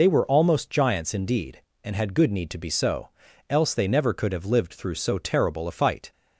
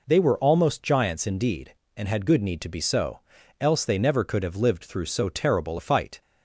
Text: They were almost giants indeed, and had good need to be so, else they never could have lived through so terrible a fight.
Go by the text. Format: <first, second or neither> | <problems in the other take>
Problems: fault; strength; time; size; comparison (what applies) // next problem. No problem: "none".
second | loses the start of "They"; at 0.0 s; 60 ms